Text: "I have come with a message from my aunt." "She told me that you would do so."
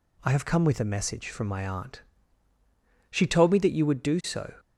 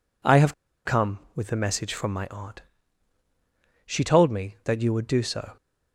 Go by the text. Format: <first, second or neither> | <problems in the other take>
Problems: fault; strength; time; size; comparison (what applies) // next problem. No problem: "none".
first | pauses between "have" and "come"; slight; at 0.5 s; 0.32 s long